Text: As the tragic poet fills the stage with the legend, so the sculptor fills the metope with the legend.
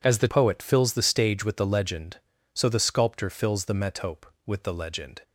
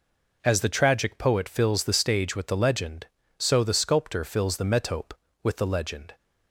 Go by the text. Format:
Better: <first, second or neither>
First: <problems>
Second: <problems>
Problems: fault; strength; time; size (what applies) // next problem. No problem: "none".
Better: second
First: skips "tragic"; at 0.2 s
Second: none